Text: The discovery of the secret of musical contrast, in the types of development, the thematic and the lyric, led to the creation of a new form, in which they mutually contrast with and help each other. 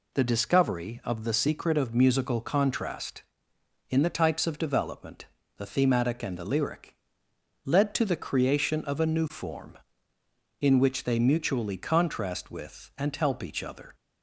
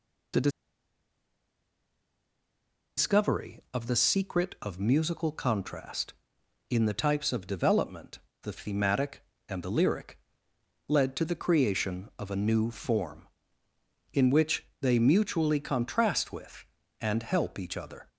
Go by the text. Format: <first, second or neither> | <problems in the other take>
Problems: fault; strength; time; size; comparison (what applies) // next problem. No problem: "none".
first | pauses between "The" and "discovery"; strong; at 0.5 s; 2.4 s long // pauses between "which" and "they"; slight; at 14.6 s; 0.16 s long